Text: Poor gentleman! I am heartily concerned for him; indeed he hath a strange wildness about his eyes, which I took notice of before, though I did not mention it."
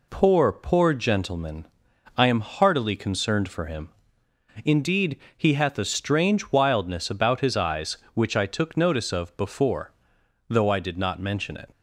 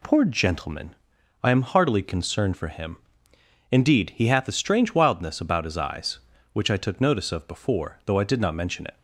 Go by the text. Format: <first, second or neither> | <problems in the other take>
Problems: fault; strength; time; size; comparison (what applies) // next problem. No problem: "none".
second | says "Poor" twice; at 0.5 s // pauses between "indeed" and "he"; slight; at 5.1 s; 0.18 s long